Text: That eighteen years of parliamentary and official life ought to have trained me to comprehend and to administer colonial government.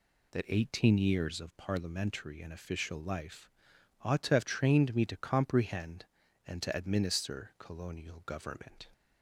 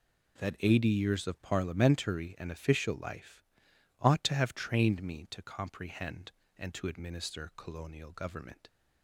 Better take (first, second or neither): first